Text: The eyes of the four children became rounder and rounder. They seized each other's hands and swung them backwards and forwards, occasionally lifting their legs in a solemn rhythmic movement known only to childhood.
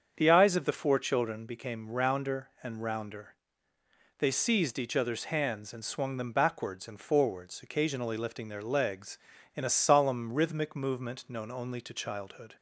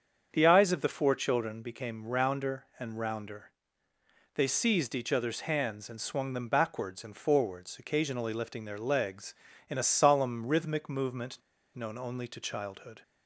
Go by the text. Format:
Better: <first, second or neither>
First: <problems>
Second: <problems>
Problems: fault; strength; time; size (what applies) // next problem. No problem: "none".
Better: first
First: starts louder than the rest; strong; until 1.1 s; 7 dB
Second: starts louder than the rest; strong; until 1.3 s; 7 dB // pauses between "movement" and "known"; slight; at 11.3 s; 0.35 s long